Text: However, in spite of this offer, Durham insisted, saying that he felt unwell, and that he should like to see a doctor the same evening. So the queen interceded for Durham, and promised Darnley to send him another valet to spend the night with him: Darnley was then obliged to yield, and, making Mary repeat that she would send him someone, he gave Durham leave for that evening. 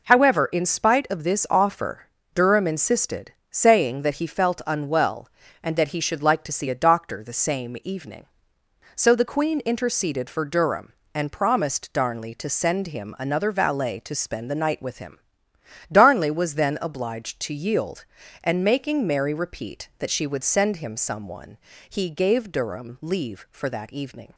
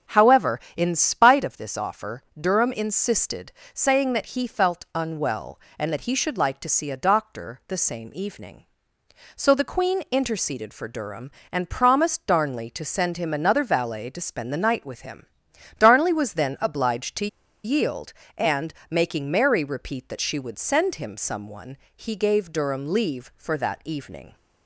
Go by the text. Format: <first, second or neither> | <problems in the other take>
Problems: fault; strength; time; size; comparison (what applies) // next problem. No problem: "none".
first | starts louder than the rest; strong; until 1.2 s; 8 dB // pauses between "to" and "yield"; at 17.2 s; 0.37 s long